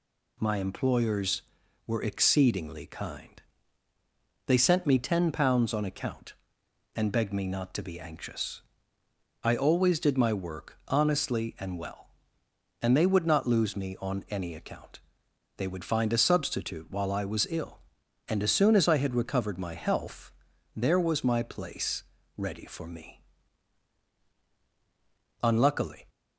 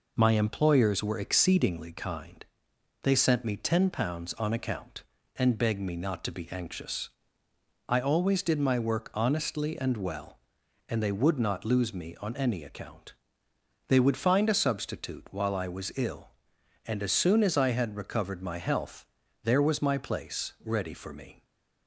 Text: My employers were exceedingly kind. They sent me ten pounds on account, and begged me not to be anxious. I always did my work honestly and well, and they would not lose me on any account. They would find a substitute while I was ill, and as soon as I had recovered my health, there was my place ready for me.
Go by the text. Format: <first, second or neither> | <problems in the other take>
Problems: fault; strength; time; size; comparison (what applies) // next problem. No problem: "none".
second | pauses between "place" and "ready"; slight; at 22.0 s; 0.34 s long // goes on to say "Unluckily"; noticeable; from 25.4 s on; 0.62 s long